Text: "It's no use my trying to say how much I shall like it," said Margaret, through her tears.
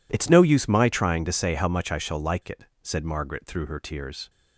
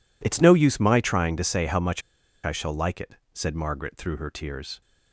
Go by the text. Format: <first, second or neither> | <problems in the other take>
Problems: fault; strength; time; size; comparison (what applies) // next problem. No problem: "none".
first | pauses between "much" and "I"; at 2.0 s; 0.45 s long